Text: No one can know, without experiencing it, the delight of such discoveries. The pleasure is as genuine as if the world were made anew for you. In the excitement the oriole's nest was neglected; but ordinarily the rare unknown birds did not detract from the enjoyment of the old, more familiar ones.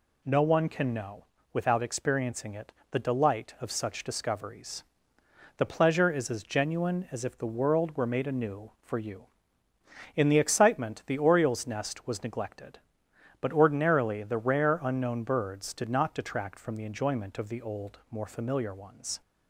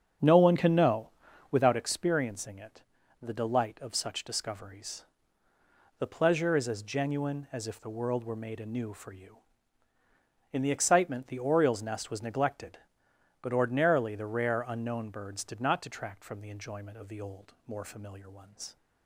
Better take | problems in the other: first | starts louder than the rest; strong; until 1.9 s; 7.5 dB

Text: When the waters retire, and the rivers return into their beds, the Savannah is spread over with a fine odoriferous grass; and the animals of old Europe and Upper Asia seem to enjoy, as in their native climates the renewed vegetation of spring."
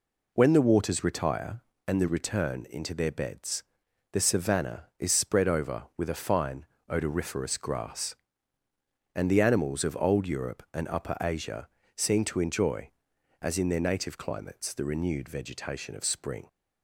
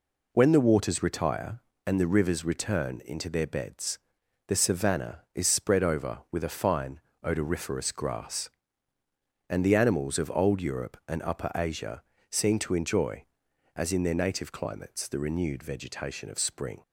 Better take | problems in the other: second | skips "rivers"; at 2.0 s // pauses between "fine" and "odoriferous"; slight; at 6.6 s; 0.24 s long; slight in the second // pauses between "Asia" and "seem"; slight; at 11.6 s; 0.28 s long; slight in the second

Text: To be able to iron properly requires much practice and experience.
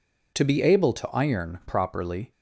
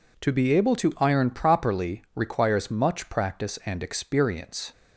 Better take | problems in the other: second | stops before "requires much practice and experience"; at 2.3 s

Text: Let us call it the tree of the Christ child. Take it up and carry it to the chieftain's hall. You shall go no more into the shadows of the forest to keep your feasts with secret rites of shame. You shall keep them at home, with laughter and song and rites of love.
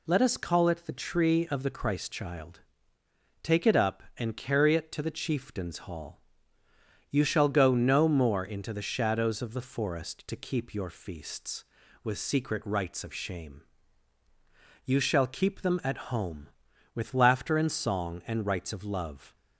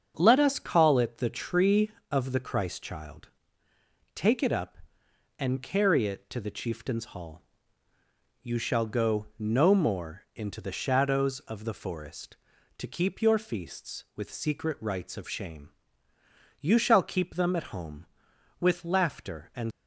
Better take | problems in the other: first | starts louder than the rest; until 1.1 s; 7 dB // stops before "song and rites of love"; at 19.7 s

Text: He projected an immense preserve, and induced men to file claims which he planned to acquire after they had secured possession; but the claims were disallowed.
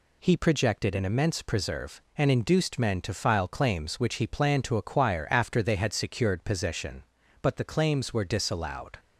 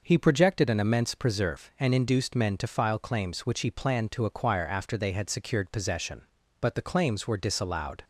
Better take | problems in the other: neither | none

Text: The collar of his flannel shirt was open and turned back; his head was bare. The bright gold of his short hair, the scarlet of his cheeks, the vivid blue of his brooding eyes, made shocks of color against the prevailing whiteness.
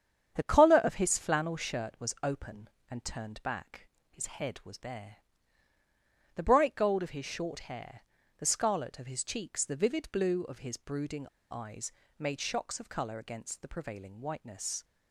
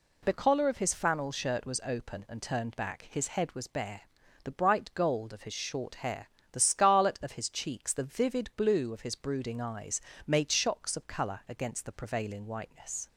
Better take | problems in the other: second | starts louder than the rest; strong; until 1.3 s; 8.5 dB // pauses between "brooding" and "eyes"; slight; at 11.2 s; 0.23 s long

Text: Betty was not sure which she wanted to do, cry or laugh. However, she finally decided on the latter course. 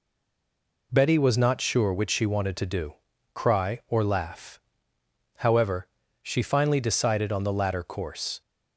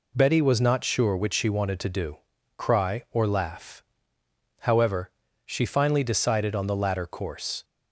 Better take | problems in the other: second | stays silent before the first word; slight; until 0.9 s; 0.9 s long

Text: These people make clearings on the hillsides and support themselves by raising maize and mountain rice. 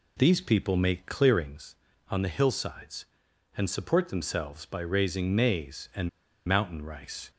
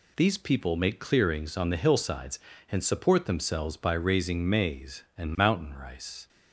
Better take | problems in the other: second | pauses between "and" and "mountain"; at 6.0 s; 0.36 s long

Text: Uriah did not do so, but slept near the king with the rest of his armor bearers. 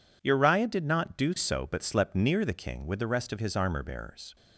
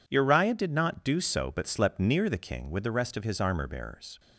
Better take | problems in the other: neither | none

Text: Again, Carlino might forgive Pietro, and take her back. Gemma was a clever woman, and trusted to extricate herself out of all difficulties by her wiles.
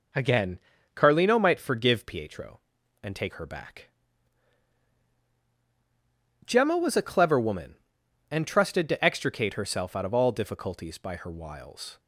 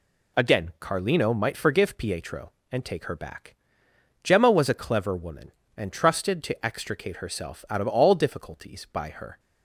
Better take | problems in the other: first | stops before "wiles"; at 9.3 s

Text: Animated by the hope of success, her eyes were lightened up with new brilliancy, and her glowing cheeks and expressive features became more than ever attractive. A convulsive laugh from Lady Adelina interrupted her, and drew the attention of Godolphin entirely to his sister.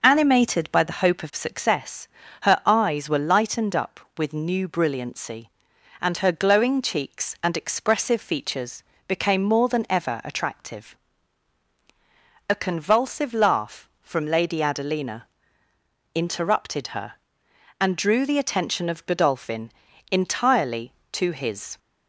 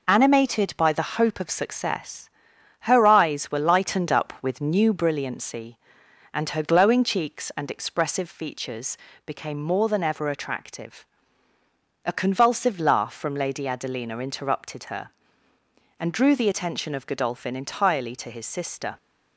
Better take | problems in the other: second | pauses between "features" and "became"; slight; at 8.8 s; 0.26 s long; slight in the second // pauses between "Adelina" and "interrupted"; noticeable; at 15.2 s; 0.88 s long // pauses between "Godolphin" and "entirely"; at 19.6 s; 0.40 s long // stops before "sister"; at 21.7 s

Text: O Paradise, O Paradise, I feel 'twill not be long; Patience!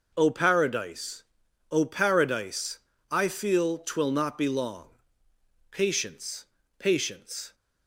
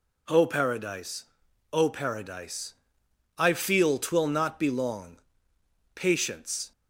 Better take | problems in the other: second | says "Patience" twice; at 6.7 s

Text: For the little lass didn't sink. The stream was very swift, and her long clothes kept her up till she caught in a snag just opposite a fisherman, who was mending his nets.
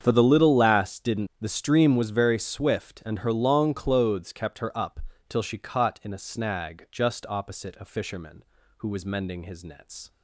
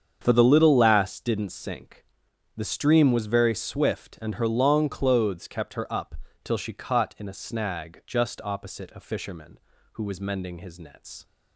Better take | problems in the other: second | starts louder than the rest; strong; until 1.0 s; 7.5 dB; strong in the second // skips "sink"; at 1.3 s // pauses between "up" and "till"; slight; at 4.9 s; 0.30 s long; slight in the second

